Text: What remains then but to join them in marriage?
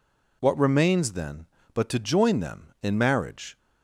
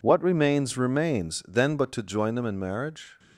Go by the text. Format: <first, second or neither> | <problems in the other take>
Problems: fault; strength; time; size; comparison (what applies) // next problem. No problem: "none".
first | says "remains" twice; at 0.7 s